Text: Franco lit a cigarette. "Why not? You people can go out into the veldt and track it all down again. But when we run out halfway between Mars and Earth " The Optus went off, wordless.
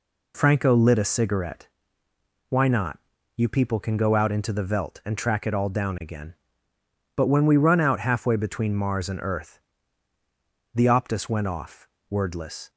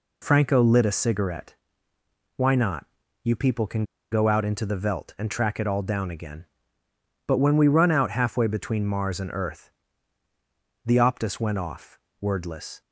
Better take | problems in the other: first | pauses between "can" and "go"; slight; at 3.8 s; 0.28 s long

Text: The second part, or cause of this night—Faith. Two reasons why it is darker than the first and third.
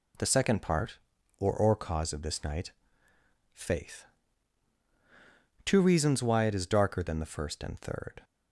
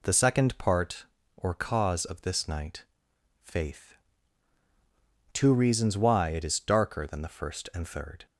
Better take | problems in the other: second | says "or" twice; at 1.5 s

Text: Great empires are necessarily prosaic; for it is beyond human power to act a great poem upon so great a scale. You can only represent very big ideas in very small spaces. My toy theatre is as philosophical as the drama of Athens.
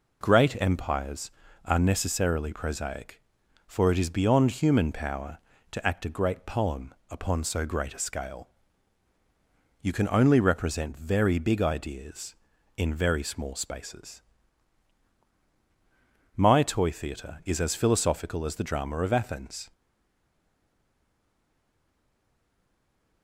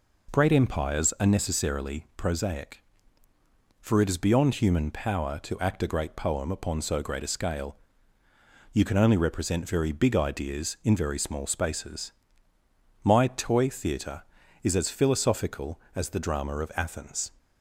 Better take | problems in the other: second | pauses between "poem" and "upon"; slight; at 6.9 s; 0.16 s long // stays silent after the last word; strong; from 19.7 s on; 3.5 s long

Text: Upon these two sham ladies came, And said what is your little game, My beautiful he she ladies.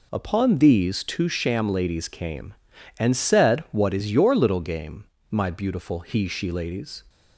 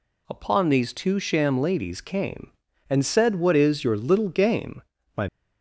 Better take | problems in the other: first | stops before "beautiful he she ladies"; at 5.2 s

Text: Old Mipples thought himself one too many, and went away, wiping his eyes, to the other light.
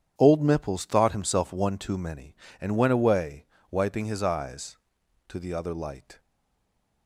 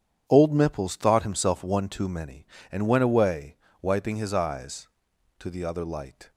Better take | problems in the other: second | starts louder than the rest; strong; until 1.1 s; 9 dB; strong in the second // stays silent after the last word; slight; from 6.1 s on; 0.9 s long

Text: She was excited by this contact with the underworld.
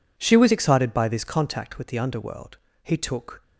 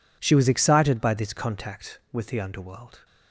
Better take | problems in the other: second | goes on to say "He took"; from 2.8 s on; 0.58 s long

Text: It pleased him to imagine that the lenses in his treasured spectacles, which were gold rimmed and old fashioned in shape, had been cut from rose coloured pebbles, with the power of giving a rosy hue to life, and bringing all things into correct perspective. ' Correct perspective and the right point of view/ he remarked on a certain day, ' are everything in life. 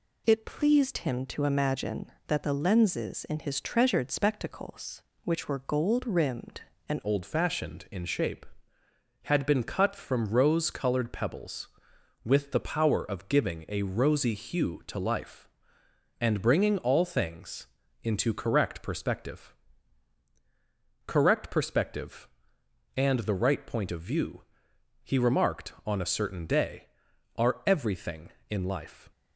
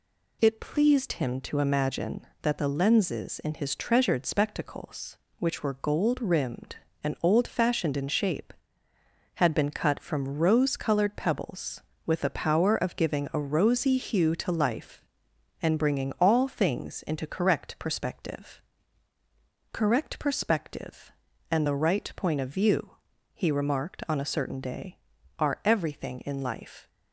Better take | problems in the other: second | changes voice at "old"; from 7.0 s on; 22.1 s long // pauses between "things" and "into"; slight; at 17.6 s; 0.34 s long

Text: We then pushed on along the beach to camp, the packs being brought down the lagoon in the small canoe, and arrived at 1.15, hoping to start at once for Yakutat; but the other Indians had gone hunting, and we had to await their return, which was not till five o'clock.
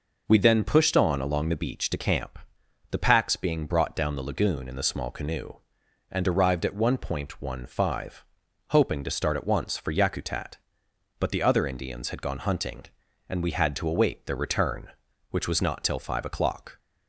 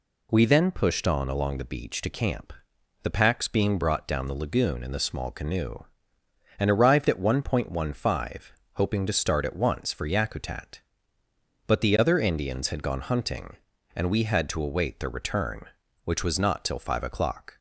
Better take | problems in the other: neither | none

